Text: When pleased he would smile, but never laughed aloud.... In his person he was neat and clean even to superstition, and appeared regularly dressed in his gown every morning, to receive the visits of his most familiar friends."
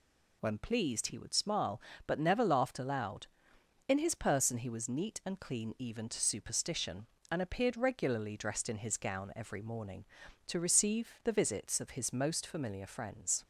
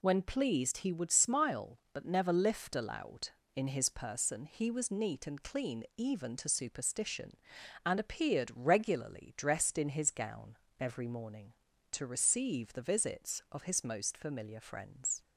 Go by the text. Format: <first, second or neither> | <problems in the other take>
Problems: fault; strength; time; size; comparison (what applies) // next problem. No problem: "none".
first | says "lift" for "laughed"; at 2.3 s // pauses between "gown" and "every"; slight; at 10.5 s; 0.22 s long